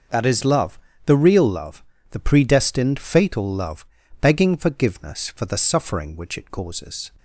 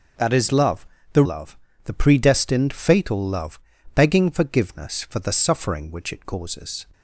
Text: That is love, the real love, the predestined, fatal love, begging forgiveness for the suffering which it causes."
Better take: first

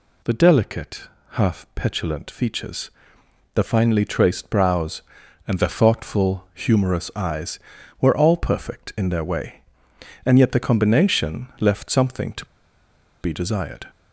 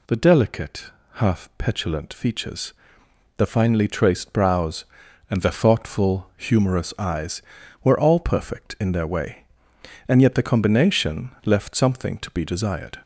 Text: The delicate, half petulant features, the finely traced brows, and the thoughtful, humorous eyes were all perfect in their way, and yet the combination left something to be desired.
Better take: second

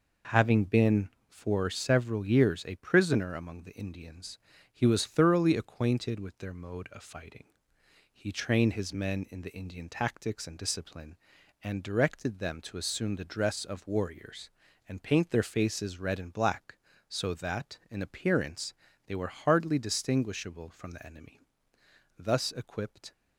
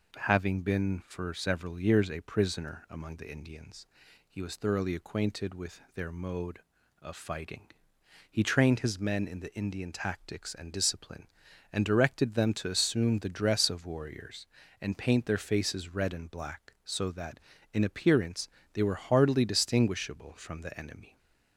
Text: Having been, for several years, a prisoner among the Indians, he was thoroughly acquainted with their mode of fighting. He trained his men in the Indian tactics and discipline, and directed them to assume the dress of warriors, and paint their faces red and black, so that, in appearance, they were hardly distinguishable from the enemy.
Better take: second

